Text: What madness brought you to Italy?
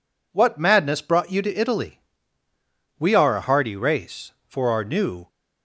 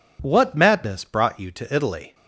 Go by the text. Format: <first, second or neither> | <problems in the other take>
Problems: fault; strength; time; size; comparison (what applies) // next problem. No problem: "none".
second | goes on to say "We are a hardy race for our new"; strong; from 2.9 s on; 2.3 s long